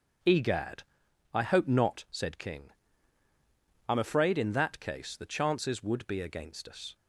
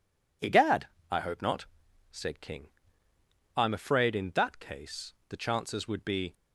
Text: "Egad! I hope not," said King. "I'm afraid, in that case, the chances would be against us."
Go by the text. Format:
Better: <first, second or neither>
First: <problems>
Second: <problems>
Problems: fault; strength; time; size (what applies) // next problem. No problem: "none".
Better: first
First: none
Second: stops before "against us"; at 6.3 s